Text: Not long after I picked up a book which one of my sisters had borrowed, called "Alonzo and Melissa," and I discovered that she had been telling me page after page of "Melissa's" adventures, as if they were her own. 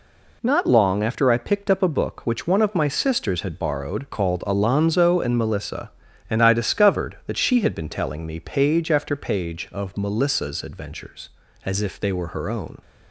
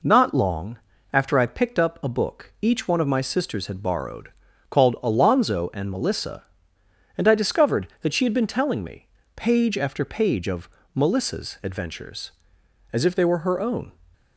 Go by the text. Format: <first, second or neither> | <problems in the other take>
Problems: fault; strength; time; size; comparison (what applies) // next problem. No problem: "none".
first | pauses between "long" and "after"; slight; at 0.7 s; 0.34 s long // says "each" for "which"; at 2.6 s // pauses between "me" and "page"; slight; at 9.0 s; 0.26 s long // pauses between "of" and "Melissa's"; slight; at 10.7 s; 0.24 s long